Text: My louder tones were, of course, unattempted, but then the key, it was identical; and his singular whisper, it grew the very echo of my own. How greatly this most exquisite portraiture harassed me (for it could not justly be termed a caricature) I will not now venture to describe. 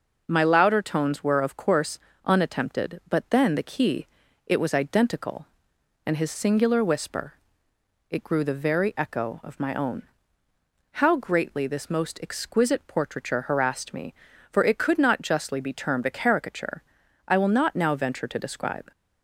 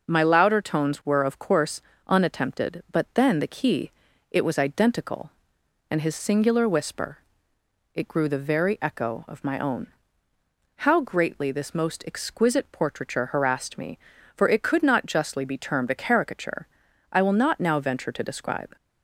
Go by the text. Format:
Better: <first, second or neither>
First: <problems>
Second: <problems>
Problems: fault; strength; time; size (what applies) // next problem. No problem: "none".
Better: neither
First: none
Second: none